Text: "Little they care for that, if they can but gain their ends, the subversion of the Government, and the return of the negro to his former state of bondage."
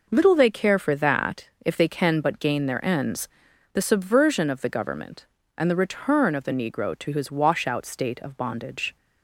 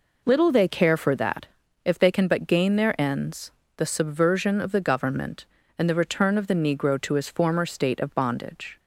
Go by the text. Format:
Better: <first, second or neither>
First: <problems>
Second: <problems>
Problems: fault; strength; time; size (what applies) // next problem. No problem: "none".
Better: second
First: says "washout" for "former"; at 7.2 s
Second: none